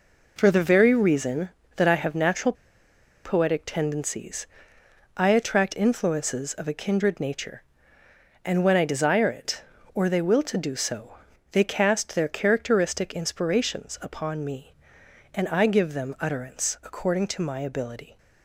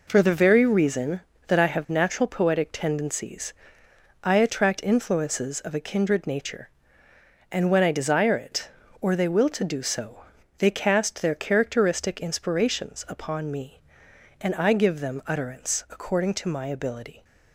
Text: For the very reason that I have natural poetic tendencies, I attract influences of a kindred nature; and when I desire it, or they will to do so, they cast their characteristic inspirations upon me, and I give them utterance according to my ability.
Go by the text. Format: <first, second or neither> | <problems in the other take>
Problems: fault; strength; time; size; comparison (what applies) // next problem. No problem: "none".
second | pauses between "natural" and "poetic"; noticeable; at 2.5 s; 0.71 s long